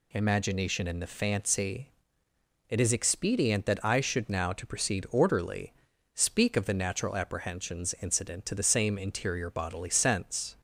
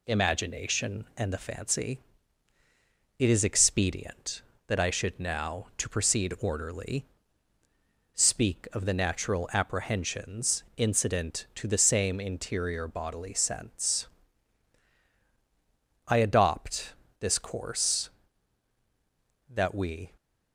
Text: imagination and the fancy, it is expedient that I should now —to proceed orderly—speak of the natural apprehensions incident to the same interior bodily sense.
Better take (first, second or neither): first